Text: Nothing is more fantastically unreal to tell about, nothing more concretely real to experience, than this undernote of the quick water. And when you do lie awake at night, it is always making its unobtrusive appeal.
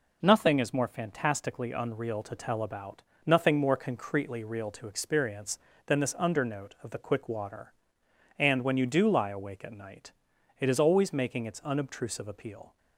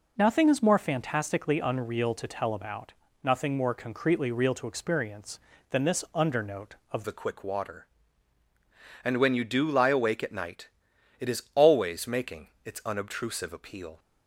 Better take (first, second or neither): first